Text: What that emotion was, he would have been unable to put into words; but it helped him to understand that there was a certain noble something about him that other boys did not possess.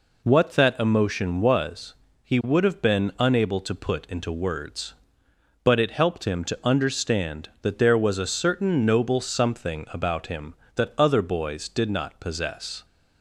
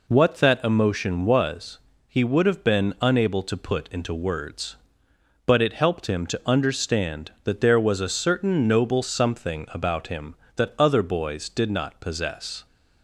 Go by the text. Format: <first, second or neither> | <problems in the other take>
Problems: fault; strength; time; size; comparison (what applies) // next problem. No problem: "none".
neither | none